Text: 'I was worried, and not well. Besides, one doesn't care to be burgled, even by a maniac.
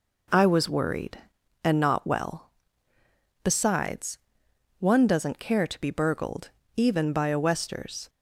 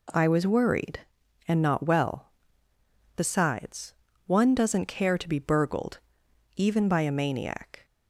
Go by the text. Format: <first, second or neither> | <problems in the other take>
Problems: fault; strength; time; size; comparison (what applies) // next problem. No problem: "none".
second | says "westers" for "maniac"; at 7.3 s